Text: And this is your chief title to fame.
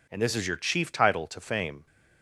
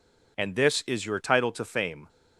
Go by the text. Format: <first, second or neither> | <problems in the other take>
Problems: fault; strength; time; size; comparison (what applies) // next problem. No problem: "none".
first | skips "chief"; at 1.2 s